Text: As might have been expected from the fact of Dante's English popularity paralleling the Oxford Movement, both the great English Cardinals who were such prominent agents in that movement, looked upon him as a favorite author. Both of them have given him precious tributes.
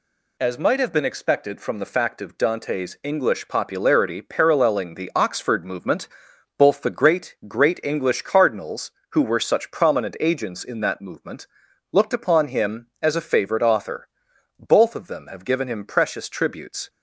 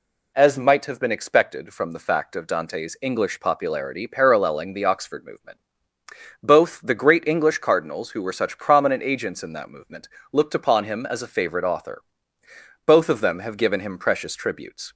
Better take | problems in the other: second | says "great" twice; at 7.4 s

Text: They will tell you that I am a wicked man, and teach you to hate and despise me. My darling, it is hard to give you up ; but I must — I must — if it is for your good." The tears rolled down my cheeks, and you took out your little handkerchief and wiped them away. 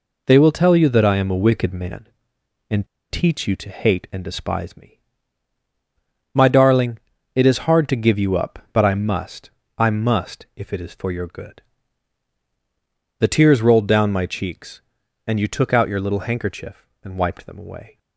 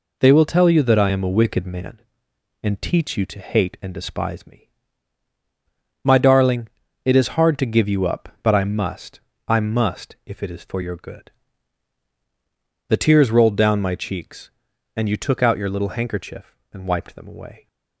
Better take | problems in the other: second | pauses between "and" and "teach"; slight; at 2.8 s; 0.23 s long

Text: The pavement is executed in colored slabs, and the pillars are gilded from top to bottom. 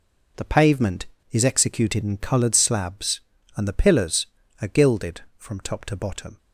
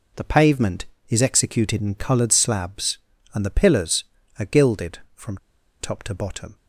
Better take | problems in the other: first | pauses between "from" and "top"; at 5.3 s; 0.43 s long

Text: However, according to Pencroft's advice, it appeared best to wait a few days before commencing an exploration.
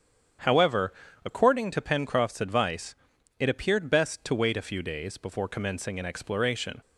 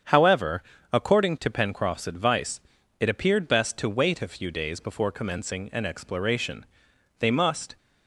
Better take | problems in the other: first | starts louder than the rest; strong; until 1.3 s; 7.5 dB; strong in the first // goes on to say "They must"; from 7.1 s on; 0.58 s long

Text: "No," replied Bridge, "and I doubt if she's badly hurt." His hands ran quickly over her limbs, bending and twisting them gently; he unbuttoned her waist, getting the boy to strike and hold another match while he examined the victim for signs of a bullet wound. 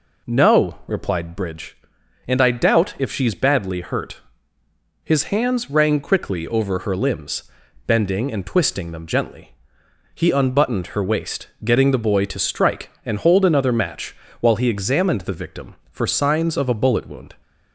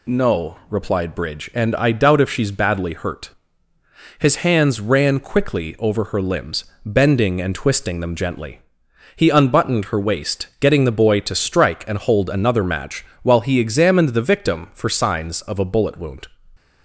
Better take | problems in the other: second | says "rang" for "ran"; at 5.6 s // pauses between "match" and "while"; slight; at 14.1 s; 0.24 s long; slight in the second

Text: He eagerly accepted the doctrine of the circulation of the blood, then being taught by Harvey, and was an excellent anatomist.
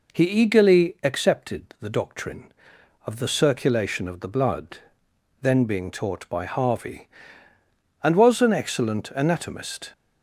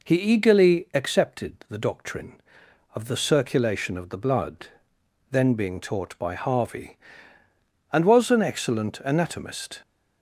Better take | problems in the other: neither | none

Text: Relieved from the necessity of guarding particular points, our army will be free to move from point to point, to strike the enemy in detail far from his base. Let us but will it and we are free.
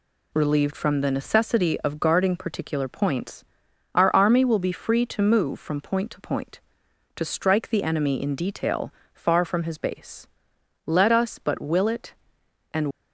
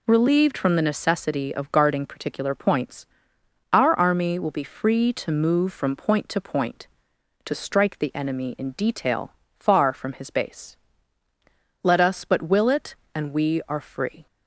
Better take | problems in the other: second | pauses between "detail" and "far"; slight; at 8.9 s; 0.18 s long; slight in the second // stops before "we are free"; at 12.9 s

